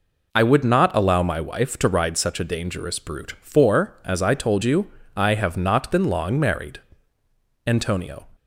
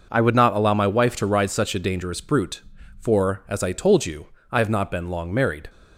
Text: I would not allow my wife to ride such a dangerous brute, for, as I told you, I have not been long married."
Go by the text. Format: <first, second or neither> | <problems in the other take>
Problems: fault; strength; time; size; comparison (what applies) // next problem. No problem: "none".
second | goes on to say "Antonio"; from 7.6 s on; 0.60 s long